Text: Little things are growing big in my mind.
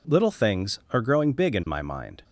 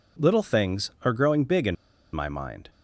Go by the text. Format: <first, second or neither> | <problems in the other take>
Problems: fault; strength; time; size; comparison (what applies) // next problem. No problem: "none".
first | pauses between "in" and "my"; at 1.7 s; 0.37 s long